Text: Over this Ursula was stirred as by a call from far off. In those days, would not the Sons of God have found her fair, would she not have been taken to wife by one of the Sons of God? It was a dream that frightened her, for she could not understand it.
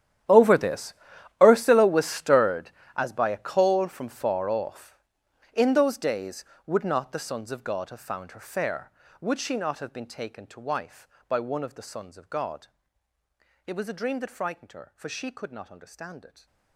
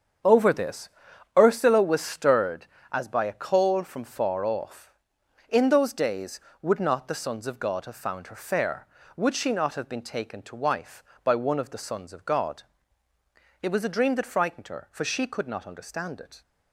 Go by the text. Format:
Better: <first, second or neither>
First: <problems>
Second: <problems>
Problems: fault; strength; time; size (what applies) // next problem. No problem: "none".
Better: second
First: gets quieter; strong; throughout; 19 dB // starts louder than the rest; strong; until 1.7 s; 11 dB // pauses between "this" and "Ursula"; noticeable; at 0.9 s; 0.48 s long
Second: starts louder than the rest; strong; until 1.7 s; 7.5 dB // pauses between "this" and "Ursula"; noticeable; at 0.8 s; 0.48 s long